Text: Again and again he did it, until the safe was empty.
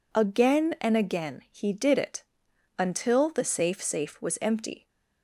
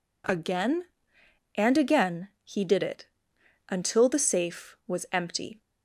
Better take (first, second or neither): second